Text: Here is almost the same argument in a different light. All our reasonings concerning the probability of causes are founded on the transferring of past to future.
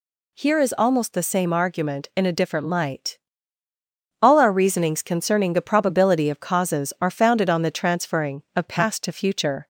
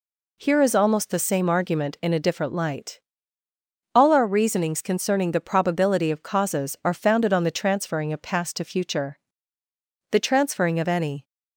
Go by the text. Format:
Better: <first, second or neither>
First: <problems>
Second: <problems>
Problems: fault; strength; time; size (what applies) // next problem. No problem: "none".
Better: first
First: none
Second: goes on to say "The transferring of any"; noticeable; from 10.1 s on; 1.1 s long